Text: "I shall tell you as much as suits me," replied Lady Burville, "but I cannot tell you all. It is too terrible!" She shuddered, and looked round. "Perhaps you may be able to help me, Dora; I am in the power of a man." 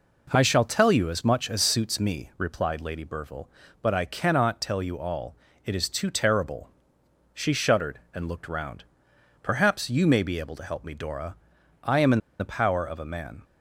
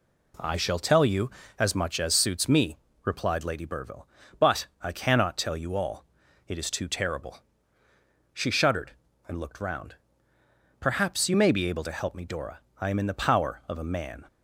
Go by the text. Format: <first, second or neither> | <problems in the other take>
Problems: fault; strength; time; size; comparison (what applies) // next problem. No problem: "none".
second | pauses between "in" and "the"; slight; at 12.1 s; 0.21 s long